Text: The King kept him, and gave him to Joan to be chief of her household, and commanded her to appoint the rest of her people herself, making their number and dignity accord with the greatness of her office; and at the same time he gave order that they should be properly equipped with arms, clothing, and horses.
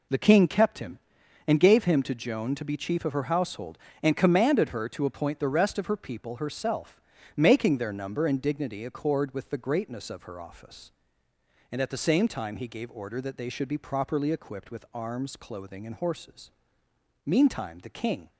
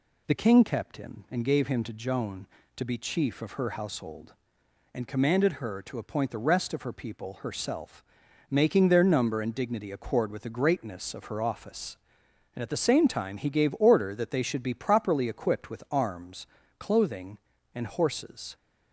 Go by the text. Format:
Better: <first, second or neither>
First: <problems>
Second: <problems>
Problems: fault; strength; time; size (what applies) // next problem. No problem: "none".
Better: second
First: goes on to say "Meantime the King"; noticeable; from 17.2 s on; 1.0 s long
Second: none